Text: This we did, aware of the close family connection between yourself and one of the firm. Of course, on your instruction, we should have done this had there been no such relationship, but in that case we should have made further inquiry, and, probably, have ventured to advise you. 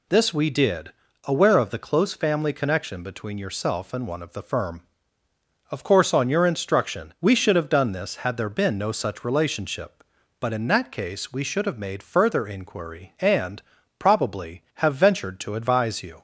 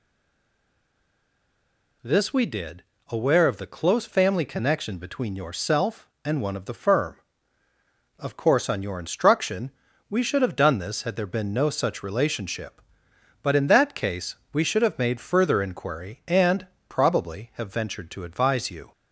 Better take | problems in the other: first | stays silent before the first word; noticeable; until 2.0 s; 2.0 s long // pauses between "case" and "we"; slight; at 14.3 s; 0.18 s long

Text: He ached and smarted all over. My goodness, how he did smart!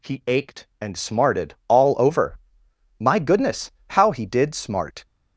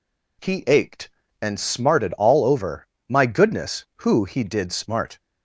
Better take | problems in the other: first | says "who" for "how"; at 4.0 s

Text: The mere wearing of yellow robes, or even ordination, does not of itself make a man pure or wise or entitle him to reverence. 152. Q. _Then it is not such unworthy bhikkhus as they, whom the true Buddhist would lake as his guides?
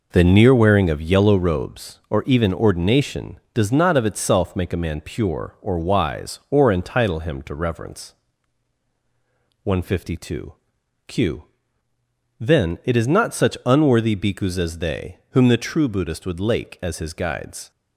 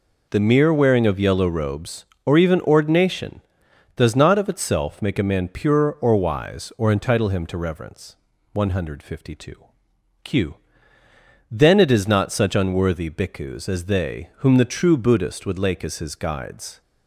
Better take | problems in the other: second | says "near" for "mere"; at 0.2 s

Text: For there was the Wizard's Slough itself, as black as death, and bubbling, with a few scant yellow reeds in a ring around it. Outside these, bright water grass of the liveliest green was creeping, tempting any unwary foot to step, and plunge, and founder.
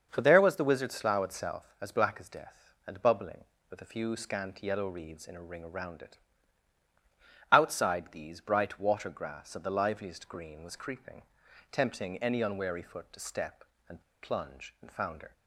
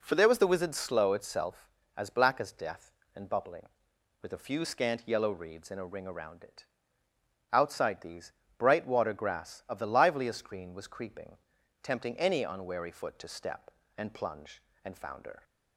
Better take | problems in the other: second | starts louder than the rest; until 1.1 s; 6.5 dB // pauses between "and" and "plunge"; slight; at 14.0 s; 0.20 s long

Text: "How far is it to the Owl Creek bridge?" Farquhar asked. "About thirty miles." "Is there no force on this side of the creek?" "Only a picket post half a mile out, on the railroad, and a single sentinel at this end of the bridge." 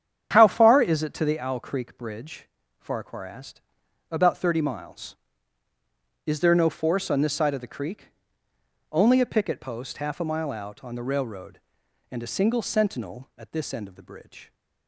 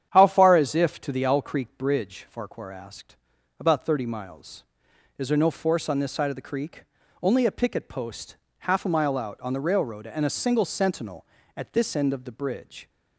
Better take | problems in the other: first | starts louder than the rest; strong; until 1.1 s; 9.5 dB; strong in the first // says "if" for "it"; at 0.7 s // pauses between "post" and "half"; slight; at 8.3 s; 0.22 s long

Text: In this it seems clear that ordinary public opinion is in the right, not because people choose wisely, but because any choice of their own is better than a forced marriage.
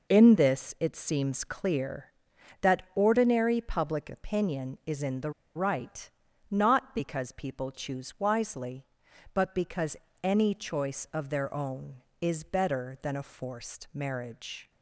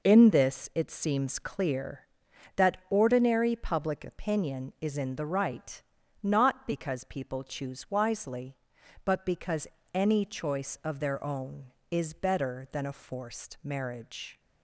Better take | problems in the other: second | pauses between "the" and "right"; slight; at 5.3 s; 0.23 s long // pauses between "because" and "any"; slight; at 9.9 s; 0.26 s long; slight in the second

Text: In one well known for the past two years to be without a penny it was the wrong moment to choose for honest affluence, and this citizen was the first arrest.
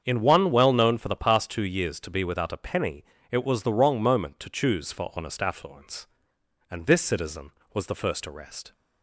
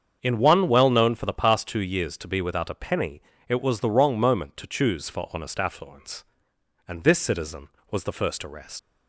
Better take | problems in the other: first | starts louder than the rest; strong; until 1.2 s; 7.5 dB; strong in the first // pauses between "penny" and "it"; slight; at 3.2 s; 0.26 s long; slight in the first // leaves "arrest" unfinished; at 8.7 s; 100 ms

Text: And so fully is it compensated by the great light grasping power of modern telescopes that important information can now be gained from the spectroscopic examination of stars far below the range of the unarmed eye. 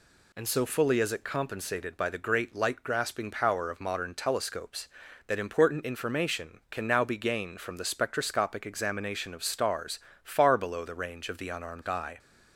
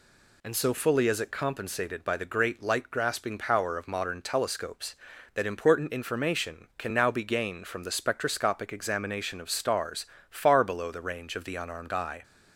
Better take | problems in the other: neither | pauses between "stars" and "far"; slight; the same in both

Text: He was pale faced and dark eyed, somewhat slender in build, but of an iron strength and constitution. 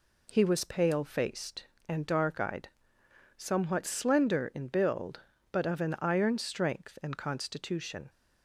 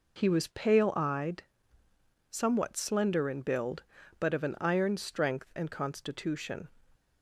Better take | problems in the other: first | skips "faced and dark"; at 0.9 s

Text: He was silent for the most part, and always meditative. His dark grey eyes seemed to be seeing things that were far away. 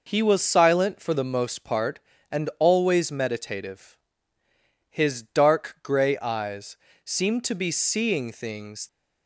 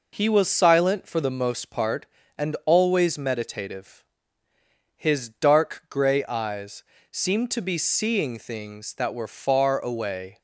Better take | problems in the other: second | pauses between "eyes" and "seemed"; slight; at 6.7 s; 0.26 s long; slight in the second // stops before "that were far away"; at 8.8 s

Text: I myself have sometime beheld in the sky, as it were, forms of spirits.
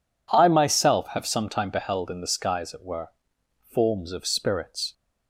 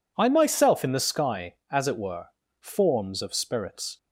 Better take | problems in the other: first | skips "have sometime beheld"; at 0.8 s

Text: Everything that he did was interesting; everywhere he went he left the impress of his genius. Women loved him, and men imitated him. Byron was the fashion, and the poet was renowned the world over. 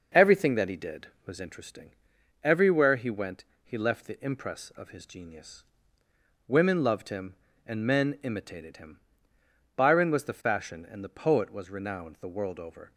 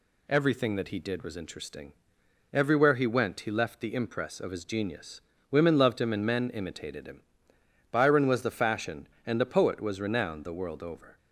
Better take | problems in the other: second | starts louder than the rest; noticeable; until 1.7 s; 6 dB // pauses between "went" and "he"; slight; at 3.4 s; 0.20 s long

